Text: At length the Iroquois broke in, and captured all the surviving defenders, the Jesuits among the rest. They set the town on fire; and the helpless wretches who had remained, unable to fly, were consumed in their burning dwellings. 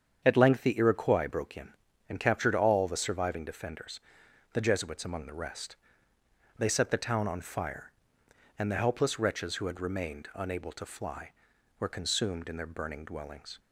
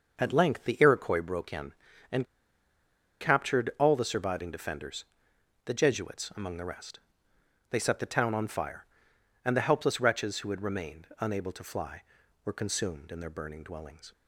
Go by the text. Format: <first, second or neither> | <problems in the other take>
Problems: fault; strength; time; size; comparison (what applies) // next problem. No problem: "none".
first | starts louder than the rest; noticeable; until 1.2 s; 6 dB; strong in the first // pauses between "and" and "captured"; noticeable; at 2.2 s; 0.95 s long